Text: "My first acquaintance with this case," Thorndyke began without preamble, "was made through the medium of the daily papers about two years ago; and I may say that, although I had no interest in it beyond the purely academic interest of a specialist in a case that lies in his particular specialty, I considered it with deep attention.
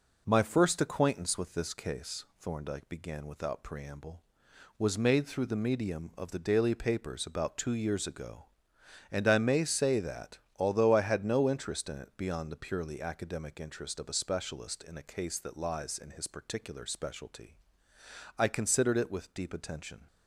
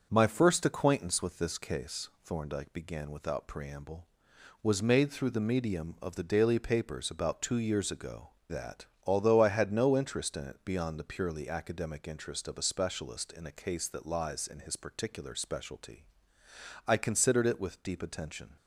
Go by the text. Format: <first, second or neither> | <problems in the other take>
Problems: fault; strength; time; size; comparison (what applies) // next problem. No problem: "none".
first | starts louder than the rest; until 1.1 s; 6.5 dB // skips "and I may say"; at 8.3 s